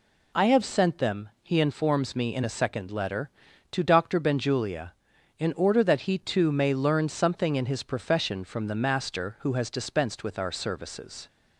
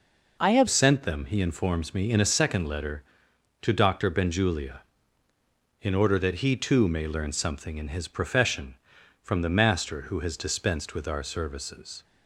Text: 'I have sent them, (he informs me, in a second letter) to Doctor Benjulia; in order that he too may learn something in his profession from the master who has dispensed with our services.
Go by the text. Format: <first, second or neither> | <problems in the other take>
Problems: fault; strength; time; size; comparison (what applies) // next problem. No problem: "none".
first | changes voice at "sent"; from 0.6 s on; 11.4 s long